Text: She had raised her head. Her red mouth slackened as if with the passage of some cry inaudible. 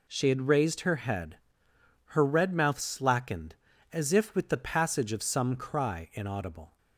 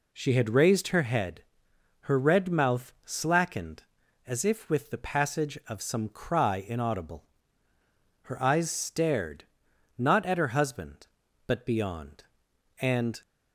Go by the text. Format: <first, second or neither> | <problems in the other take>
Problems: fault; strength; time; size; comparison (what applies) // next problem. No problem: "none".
first | goes on to say "Her eyes stared not at her husband but beyond and"; strong; from 8.2 s on; 4.9 s long